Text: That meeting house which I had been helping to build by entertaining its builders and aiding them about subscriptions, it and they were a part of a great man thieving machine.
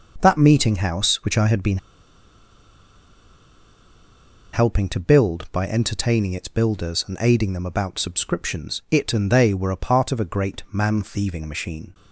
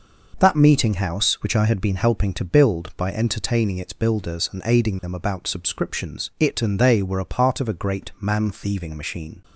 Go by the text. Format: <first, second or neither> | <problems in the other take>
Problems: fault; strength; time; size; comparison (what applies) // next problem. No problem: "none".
second | pauses between "been" and "helping"; strong; at 1.7 s; 2.7 s long